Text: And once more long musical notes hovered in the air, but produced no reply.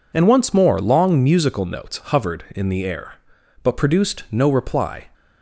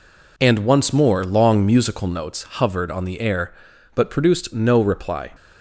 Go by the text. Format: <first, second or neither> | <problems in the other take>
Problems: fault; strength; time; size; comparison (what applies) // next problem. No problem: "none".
first | says "on" for "in"; at 2.9 s